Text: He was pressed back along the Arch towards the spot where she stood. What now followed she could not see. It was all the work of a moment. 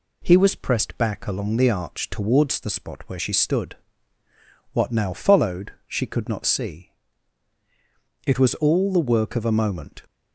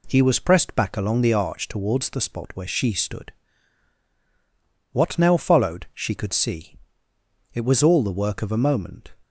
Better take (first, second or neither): first